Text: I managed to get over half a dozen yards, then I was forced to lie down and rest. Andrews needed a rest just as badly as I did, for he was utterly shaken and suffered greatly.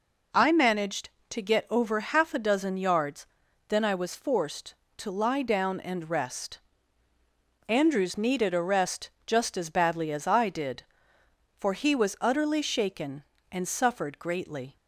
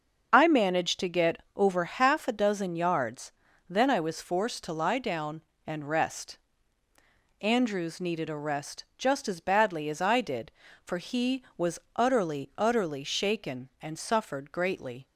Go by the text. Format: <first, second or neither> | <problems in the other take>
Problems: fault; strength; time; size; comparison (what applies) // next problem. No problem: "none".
first | starts louder than the rest; until 1.3 s; 6.5 dB // pauses between "rest" and "just"; slight; at 8.8 s; 0.16 s long; slight in the first // pauses between "was" and "utterly"; slight; at 11.7 s; 0.16 s long // says "utterly" twice; at 12.5 s